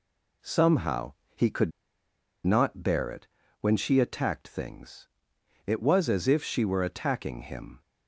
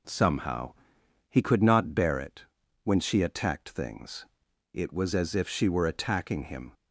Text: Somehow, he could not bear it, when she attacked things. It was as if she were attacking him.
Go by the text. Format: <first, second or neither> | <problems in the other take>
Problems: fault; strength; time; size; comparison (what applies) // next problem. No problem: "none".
second | pauses between "could" and "not"; noticeable; at 1.7 s; 0.75 s long